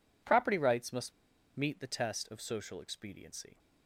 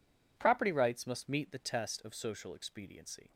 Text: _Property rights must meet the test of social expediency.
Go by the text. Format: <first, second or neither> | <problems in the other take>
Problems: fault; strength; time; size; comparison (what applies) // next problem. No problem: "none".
second | pauses between "must" and "meet"; at 1.1 s; 0.43 s long